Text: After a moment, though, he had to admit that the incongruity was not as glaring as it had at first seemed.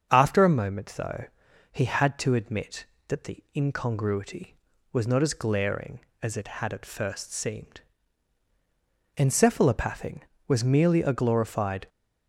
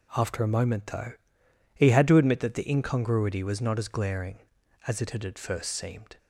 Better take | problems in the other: second | starts louder than the rest; until 1.1 s; 7 dB // goes on to say "Encephalopathing was merely a glorified"; strong; from 9.1 s on; 2.7 s long

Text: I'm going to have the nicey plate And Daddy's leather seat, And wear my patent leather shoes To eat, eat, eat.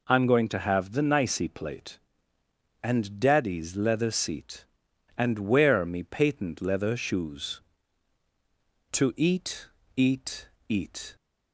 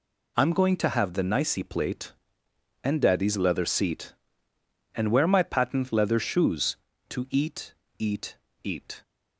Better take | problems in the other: second | says "me" for "my"; at 5.8 s

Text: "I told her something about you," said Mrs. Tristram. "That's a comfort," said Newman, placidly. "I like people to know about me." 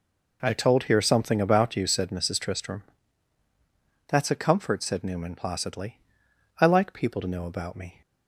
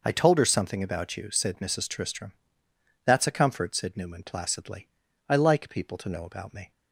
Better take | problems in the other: second | says "here" for "her"; at 0.8 s

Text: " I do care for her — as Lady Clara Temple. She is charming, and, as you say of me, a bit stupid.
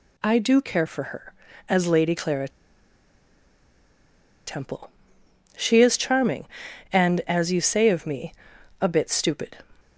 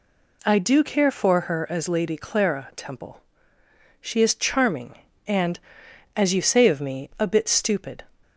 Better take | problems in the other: second | pauses between "Clara" and "Temple"; strong; at 2.4 s; 1.9 s long

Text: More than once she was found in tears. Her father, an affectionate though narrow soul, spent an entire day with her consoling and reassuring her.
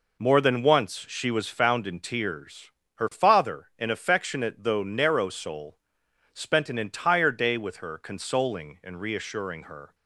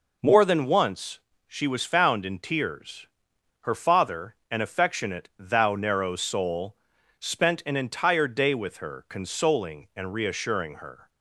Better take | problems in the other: first | pauses between "once" and "she"; slight; at 1.1 s; 0.28 s long // says "thou" for "though"; at 5.3 s

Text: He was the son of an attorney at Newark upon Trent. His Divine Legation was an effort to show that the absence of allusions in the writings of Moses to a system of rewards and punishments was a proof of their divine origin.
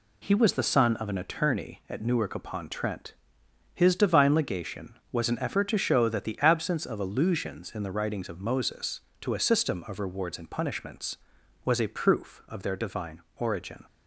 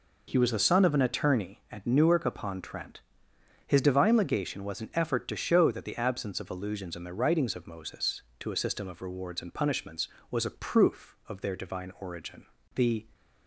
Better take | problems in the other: first | goes on to say "The"; slight; from 12.7 s on; 0.34 s long

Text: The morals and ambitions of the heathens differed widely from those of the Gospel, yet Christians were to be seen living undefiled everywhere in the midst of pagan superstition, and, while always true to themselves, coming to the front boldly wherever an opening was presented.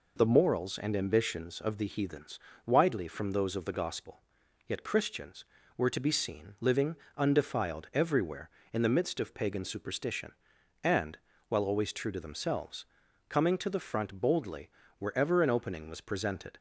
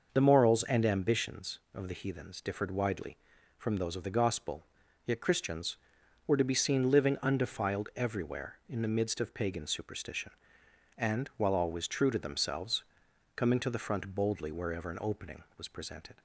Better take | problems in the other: second | skips "differed"; at 2.5 s // pauses between "living" and "undefiled"; slight; at 6.9 s; 0.22 s long // pauses between "boldly" and "wherever"; slight; at 14.7 s; 0.26 s long

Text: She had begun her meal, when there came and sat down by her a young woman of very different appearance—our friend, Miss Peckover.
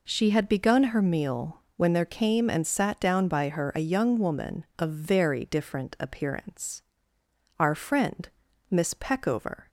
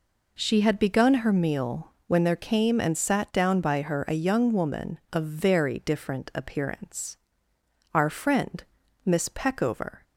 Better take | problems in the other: neither | none

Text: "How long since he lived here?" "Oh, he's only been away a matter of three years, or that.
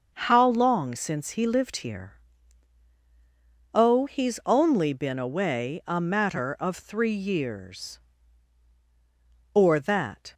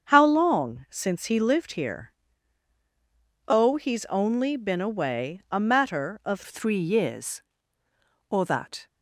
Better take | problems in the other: first | starts louder than the rest; until 1.1 s; 7 dB; also in the first // changes voice at "three"; from 6.4 s on; 2.4 s long

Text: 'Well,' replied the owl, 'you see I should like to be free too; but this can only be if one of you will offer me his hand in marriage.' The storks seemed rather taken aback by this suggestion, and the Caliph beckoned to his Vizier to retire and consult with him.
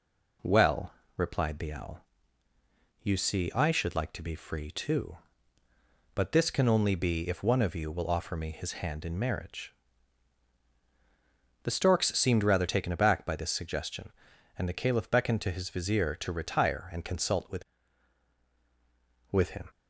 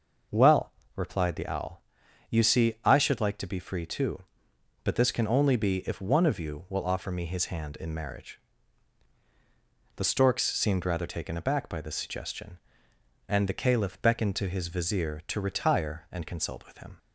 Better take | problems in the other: second | says "with" twice; at 19.3 s

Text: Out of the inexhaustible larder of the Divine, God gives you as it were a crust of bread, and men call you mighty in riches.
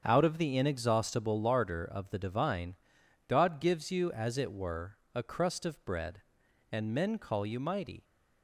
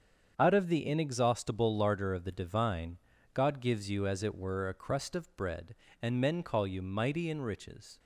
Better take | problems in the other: second | starts louder than the rest; strong; until 1.0 s; 7 dB; strong in the second // pauses between "were" and "a"; slight; at 4.9 s; 0.16 s long // stops before "in riches"; at 8.0 s

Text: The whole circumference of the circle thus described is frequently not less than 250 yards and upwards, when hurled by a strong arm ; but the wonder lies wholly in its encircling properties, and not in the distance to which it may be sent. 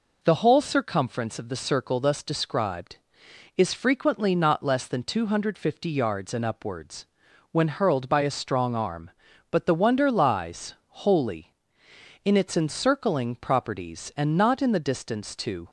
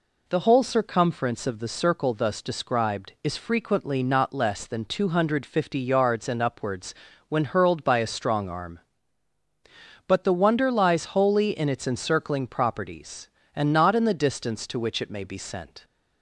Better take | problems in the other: second | stops before "which it may be sent"; at 15.6 s

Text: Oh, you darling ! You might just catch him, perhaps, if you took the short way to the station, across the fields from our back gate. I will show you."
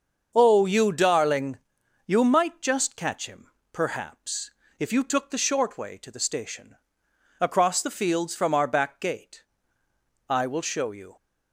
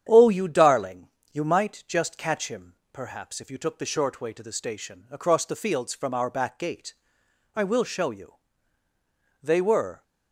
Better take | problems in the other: first | starts louder than the rest; strong; until 1.1 s; 9 dB; also in the first // goes on to say "They were"; from 9.4 s on; 0.60 s long

